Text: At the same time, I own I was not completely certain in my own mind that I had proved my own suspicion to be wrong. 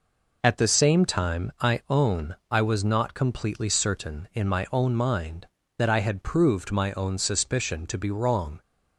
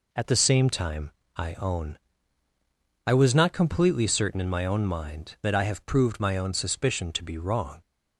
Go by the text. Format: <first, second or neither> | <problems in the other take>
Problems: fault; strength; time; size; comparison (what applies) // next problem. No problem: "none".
first | pauses between "own" and "I"; at 1.9 s; 1.1 s long; slight in the first // says "have" for "had"; at 5.6 s